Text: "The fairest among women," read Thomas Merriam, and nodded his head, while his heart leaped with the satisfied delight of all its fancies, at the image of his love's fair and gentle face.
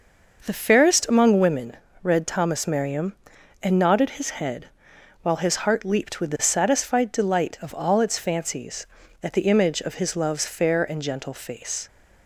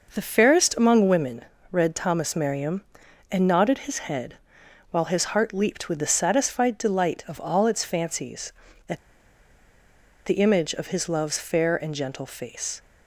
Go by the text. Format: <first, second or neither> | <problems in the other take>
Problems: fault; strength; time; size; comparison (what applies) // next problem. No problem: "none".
first | pauses between "at" and "the"; strong; at 8.9 s; 1.2 s long